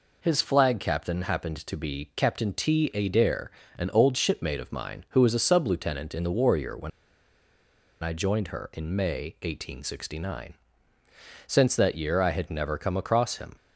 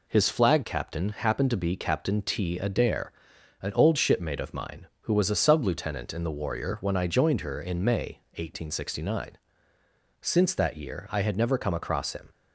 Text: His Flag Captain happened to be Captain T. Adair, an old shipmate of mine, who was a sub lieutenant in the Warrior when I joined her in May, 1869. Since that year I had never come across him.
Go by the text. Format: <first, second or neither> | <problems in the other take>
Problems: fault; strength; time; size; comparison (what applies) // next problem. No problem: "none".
second | pauses between "when" and "I"; at 6.9 s; 1.1 s long